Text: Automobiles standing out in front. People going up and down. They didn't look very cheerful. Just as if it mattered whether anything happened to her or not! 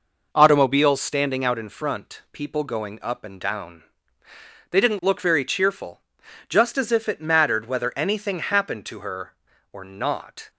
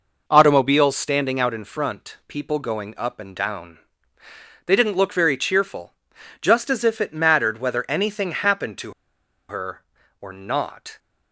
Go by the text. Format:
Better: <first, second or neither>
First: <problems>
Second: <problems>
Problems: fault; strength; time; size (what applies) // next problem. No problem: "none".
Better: first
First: none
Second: pauses between "to" and "her"; noticeable; at 8.9 s; 0.56 s long